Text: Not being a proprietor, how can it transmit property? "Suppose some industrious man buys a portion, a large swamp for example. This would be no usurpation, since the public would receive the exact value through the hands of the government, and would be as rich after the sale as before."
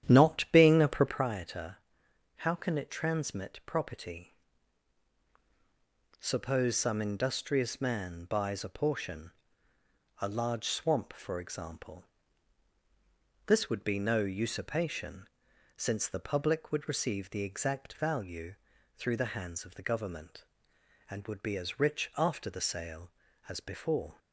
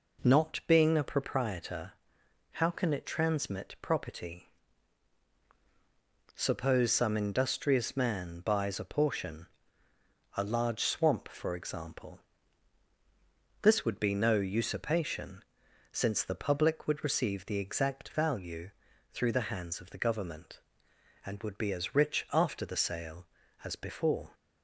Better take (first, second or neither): second